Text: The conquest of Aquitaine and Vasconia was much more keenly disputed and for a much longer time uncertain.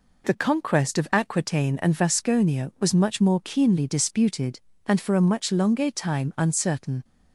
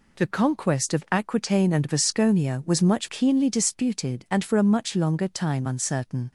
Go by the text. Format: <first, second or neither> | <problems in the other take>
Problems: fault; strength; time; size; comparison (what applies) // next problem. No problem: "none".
first | skips "more"; at 3.0 s